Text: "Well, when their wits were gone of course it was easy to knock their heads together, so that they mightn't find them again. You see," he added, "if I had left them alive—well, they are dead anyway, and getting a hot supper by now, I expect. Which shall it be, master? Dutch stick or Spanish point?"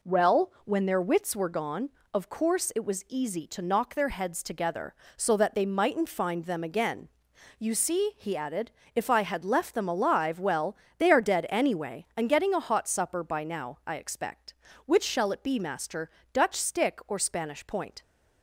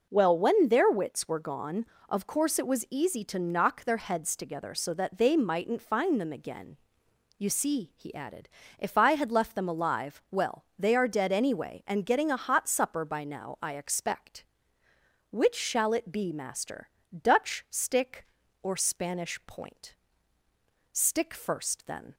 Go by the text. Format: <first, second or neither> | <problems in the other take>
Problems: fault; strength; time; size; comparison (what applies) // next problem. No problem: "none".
first | goes on to say "Stick first then"; noticeable; from 20.9 s on; 1.2 s long